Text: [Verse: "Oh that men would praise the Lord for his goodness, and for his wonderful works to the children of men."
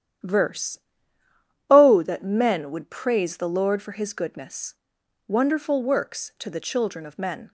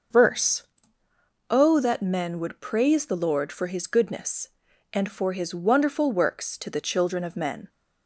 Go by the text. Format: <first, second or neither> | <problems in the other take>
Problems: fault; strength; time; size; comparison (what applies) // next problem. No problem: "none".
second | starts louder than the rest; strong; until 2.1 s; 10 dB; also in the second // skips "and for his"; at 5.0 s